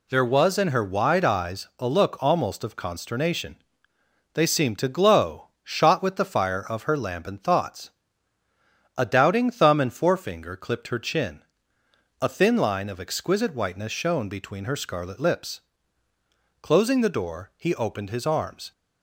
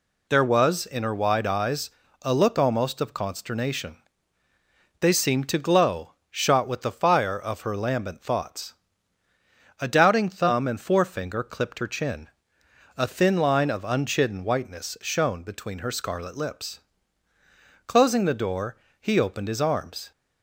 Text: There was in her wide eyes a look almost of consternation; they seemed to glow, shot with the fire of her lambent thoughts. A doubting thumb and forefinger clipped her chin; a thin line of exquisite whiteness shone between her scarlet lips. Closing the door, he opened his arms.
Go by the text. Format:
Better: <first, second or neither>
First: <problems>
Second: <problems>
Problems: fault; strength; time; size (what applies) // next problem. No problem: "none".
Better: first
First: none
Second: pauses between "eyes" and "a"; slight; at 1.8 s; 0.32 s long // says "unchidden" for "exquisite"; at 13.8 s